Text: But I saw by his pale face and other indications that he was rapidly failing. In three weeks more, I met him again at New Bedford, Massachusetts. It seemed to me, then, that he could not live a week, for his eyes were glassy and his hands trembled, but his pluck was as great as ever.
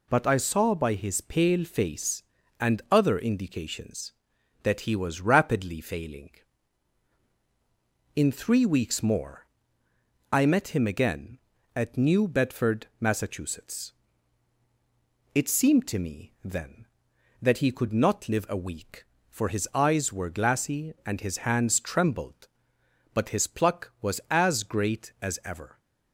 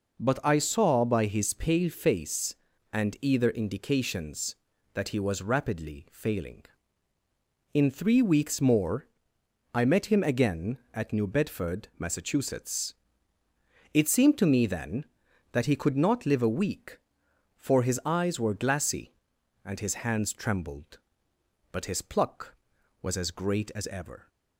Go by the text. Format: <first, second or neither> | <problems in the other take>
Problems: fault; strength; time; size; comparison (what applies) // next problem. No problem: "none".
first | says "either" for "other"; at 3.1 s